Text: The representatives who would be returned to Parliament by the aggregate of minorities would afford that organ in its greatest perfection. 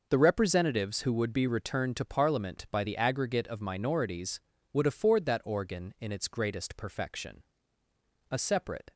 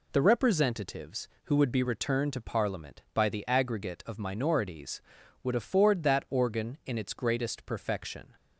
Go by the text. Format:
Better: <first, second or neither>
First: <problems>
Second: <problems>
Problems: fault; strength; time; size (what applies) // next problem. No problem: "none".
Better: second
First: goes on to say "A separate"; noticeable; from 8.3 s on; 0.62 s long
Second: none